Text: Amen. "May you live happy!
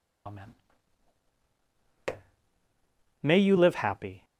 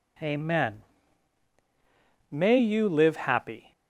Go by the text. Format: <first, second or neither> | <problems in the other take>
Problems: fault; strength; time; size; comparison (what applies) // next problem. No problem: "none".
second | loses the start of "Amen"; at 0.2 s; 75 ms